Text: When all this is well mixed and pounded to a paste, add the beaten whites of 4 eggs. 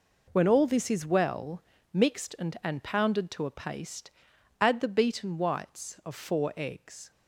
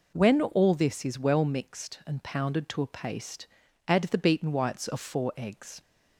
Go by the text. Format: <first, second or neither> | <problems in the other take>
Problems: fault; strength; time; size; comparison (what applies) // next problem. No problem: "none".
second | pauses between "well" and "mixed"; slight; at 1.6 s; 0.28 s long // says "and" twice; at 2.6 s